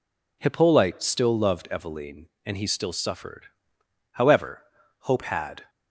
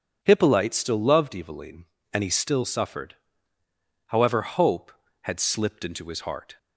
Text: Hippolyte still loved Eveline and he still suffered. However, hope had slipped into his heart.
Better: second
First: stops before "slipped into his heart"; at 5.6 s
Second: none

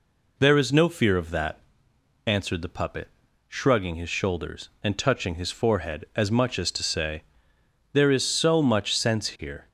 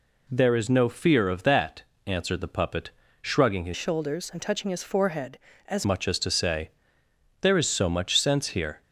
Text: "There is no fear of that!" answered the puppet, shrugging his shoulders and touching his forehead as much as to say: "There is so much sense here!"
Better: first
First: none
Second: changes voice from "shoulders" to "as"; from 3.7 to 5.8 s; 2.1 s long

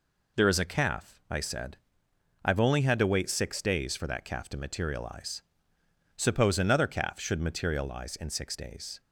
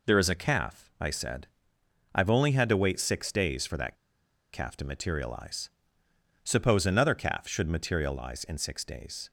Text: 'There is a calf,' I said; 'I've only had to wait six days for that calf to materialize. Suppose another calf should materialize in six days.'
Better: first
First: none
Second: pauses between "that" and "calf"; noticeable; at 3.9 s; 0.58 s long

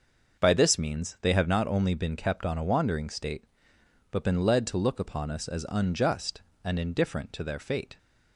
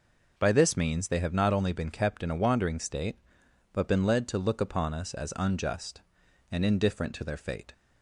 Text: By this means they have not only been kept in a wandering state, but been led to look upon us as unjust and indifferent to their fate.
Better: second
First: starts louder than the rest; until 1.4 s; 6 dB // says "on" for "in"; at 2.4 s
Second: none

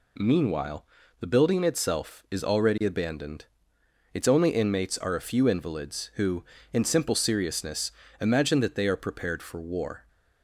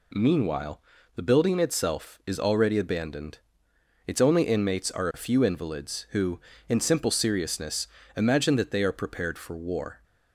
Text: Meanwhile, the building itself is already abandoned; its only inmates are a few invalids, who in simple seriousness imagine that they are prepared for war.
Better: neither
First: pauses between "seriousness" and "imagine"; slight; at 7.9 s; 0.26 s long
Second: pauses between "seriousness" and "imagine"; slight; at 7.8 s; 0.26 s long

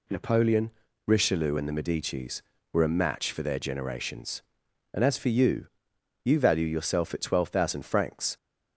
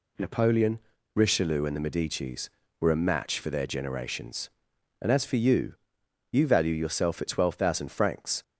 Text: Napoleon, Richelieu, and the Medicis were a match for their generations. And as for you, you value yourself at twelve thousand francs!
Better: neither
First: none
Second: none

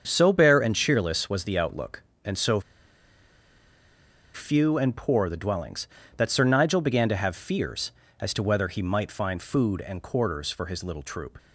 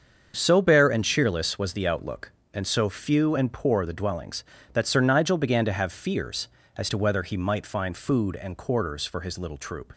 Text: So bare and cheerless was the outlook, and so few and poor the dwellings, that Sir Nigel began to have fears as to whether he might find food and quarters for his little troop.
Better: second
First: starts louder than the rest; until 1.0 s; 7 dB // pauses between "so" and "few"; strong; at 2.5 s; 1.7 s long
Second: starts louder than the rest; until 1.3 s; 7 dB

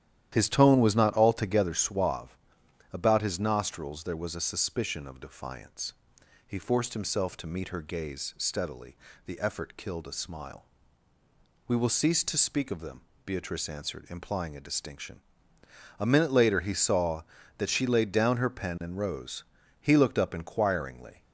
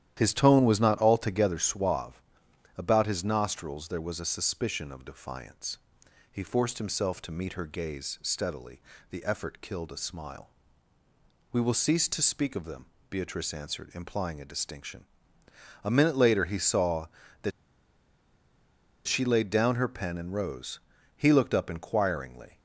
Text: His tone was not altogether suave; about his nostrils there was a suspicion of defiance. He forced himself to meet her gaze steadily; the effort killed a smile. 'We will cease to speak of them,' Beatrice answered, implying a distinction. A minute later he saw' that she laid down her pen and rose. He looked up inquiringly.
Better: first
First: starts louder than the rest; strong; until 1.3 s; 11.5 dB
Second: starts louder than the rest; strong; until 1.1 s; 11.5 dB // pauses between "that" and "she"; strong; at 17.5 s; 1.5 s long

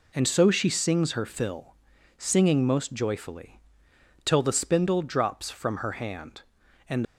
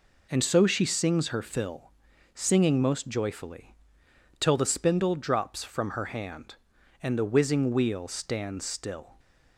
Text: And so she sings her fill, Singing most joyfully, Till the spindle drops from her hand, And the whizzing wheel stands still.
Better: second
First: stops before "the whizzing wheel stands still"; at 7.0 s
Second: none

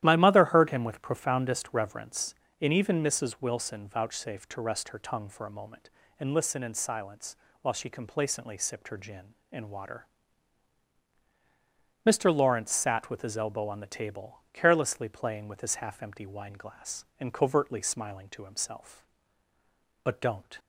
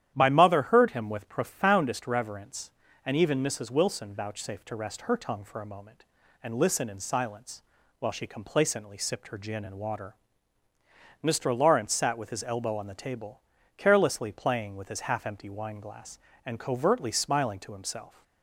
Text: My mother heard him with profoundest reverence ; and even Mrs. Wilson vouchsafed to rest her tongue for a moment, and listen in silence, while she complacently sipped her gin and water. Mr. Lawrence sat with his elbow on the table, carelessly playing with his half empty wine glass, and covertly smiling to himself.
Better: second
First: starts louder than the rest; strong; until 1.0 s; 12.5 dB // goes on to say "But don't"; from 20.0 s on; 0.54 s long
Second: starts louder than the rest; strong; until 1.1 s; 11 dB

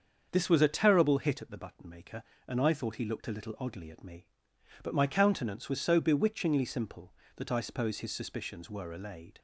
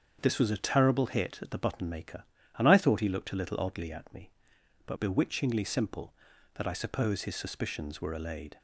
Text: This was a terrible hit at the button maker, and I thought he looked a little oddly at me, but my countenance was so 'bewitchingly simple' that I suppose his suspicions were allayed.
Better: first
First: starts louder than the rest; until 1.3 s; 7 dB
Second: starts louder than the rest; strong; until 1.2 s; 7 dB // skips "my countenance was so"; at 4.9 s

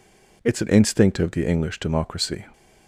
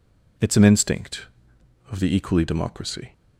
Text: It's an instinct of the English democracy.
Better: first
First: none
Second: says "Equally" for "English"; at 2.1 s

